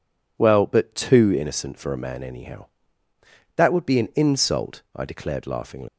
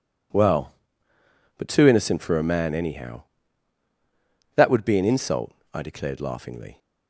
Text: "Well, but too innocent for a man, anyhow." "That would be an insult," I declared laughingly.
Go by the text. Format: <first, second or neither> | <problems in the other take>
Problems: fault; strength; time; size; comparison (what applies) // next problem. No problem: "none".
second | leaves "laughingly" unfinished; at 5.8 s; 155 ms